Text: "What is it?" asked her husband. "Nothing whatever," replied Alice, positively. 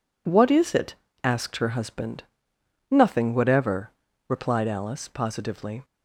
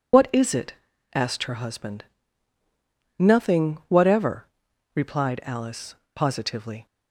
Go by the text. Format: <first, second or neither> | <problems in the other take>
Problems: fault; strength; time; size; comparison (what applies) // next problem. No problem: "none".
first | loses the start of "What"; at 0.1 s; 40 ms